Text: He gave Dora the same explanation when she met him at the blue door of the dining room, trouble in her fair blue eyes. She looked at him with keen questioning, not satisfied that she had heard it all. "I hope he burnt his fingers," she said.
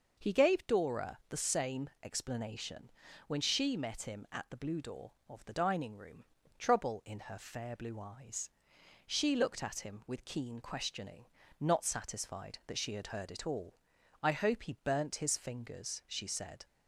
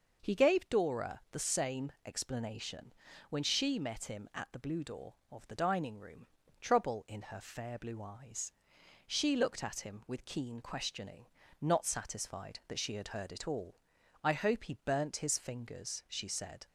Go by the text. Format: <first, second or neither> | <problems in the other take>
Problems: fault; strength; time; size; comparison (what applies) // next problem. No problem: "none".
neither | pauses between "explanation" and "when"; the same in both